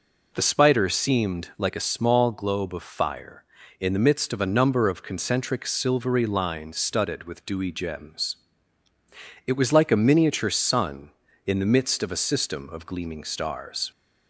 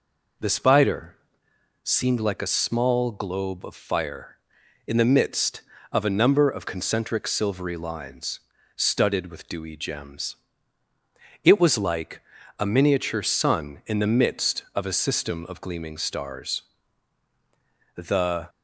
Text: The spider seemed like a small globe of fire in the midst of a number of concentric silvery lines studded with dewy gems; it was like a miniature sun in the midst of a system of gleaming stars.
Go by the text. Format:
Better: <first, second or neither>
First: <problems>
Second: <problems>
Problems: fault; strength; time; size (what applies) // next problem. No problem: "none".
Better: first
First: none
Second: pauses between "spider" and "seemed"; noticeable; at 1.1 s; 0.68 s long // pauses between "lines" and "studded"; slight; at 8.4 s; 0.34 s long // pauses between "like" and "a"; at 12.2 s; 0.38 s long // goes on to say "The"; from 17.9 s on; 0.54 s long